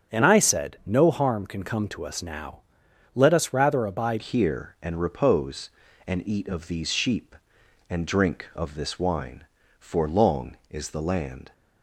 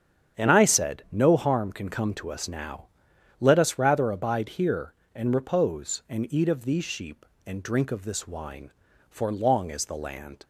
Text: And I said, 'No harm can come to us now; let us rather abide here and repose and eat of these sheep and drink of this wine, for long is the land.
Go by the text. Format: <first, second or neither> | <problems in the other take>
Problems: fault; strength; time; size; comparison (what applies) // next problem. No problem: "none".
second | starts louder than the rest; strong; until 1.1 s; 8 dB; strong in the second // changes voice at "here"; from 4.2 s on; 7.3 s long